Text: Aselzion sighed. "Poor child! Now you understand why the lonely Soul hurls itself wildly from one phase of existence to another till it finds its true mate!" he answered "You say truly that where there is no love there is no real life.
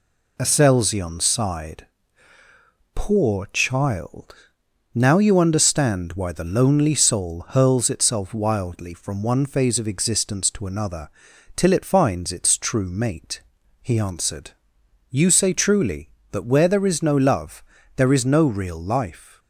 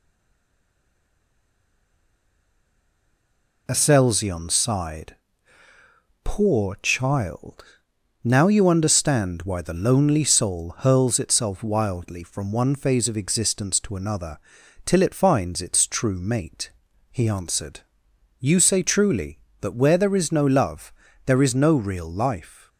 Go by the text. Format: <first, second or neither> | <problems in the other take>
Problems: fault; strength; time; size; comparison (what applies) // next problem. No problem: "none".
first | stays silent before the first word; strong; until 3.6 s; 3.6 s long // pauses between "another" and "till"; noticeable; at 14.3 s; 0.46 s long; noticeable in the first // pauses between "answered" and "You"; noticeable; at 17.8 s; 0.60 s long; noticeable in the first // pauses between "love" and "there"; slight; at 20.9 s; 0.34 s long; slight in the first